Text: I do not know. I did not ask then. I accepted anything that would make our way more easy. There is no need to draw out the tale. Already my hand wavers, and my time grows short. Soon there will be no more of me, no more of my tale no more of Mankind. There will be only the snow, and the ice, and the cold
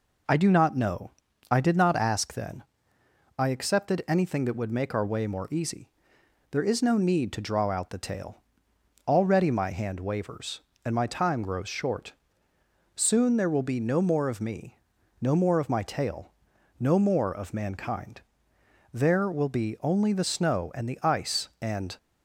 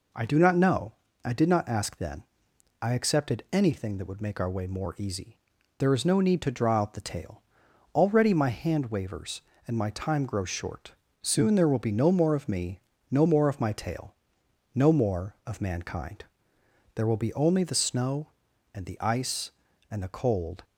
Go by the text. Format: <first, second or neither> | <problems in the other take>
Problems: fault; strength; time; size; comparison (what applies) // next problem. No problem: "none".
second | pauses between "tale" and "no"; noticeable; at 16.2 s; 0.50 s long; noticeable in the second // stops before "the cold"; at 21.9 s